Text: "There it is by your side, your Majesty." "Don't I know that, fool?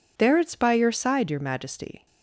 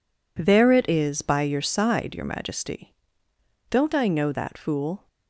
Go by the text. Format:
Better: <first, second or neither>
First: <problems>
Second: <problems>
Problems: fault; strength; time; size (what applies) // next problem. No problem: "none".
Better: second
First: stops before "Don't I know that fool"; at 2.0 s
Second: none